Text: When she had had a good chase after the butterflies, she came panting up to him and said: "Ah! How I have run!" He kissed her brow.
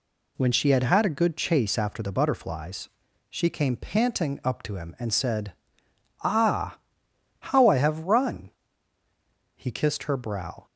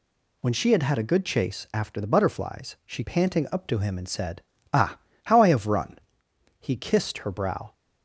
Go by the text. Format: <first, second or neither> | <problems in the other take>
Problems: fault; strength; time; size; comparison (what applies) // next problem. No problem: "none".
first | skips "came"; at 3.0 s